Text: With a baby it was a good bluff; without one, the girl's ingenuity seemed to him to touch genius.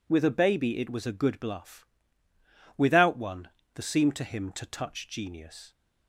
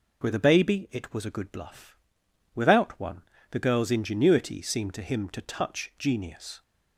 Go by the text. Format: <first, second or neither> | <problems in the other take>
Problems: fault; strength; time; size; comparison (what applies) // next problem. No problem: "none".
second | skips "girl's ingenuity"; at 3.8 s